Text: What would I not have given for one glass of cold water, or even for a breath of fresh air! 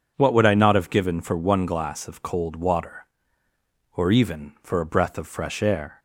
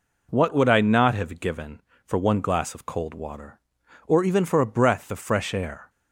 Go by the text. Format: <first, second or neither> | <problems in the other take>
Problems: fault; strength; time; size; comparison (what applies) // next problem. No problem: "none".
neither | none